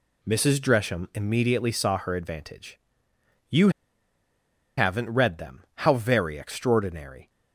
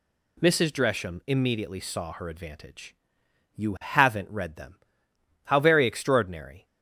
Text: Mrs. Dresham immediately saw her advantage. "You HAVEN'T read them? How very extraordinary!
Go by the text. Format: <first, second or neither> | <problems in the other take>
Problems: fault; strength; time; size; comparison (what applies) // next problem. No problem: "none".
second | pauses between "You" and "HAVEN'T"; at 3.6 s; 1.0 s long